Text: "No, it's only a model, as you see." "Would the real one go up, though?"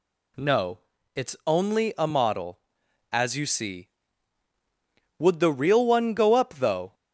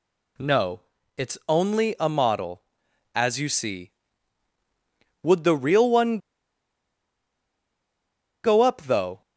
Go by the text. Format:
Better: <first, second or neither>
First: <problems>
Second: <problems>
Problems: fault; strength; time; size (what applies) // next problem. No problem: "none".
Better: first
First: none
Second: pauses between "one" and "go"; strong; at 6.1 s; 2.2 s long